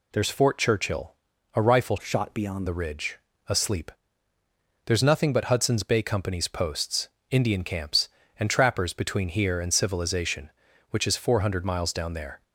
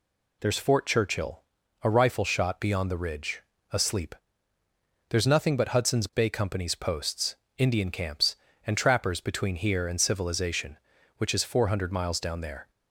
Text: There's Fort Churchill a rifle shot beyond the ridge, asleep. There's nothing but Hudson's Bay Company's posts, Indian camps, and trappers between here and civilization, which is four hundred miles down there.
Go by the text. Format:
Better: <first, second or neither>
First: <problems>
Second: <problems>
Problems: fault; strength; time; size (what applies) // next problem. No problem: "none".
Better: second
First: pauses between "Churchill" and "a"; at 1.1 s; 0.42 s long // changes voice from "shot" to "beyond"; from 2.0 to 2.6 s; 0.6 s long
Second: pauses between "Churchill" and "a"; at 1.4 s; 0.42 s long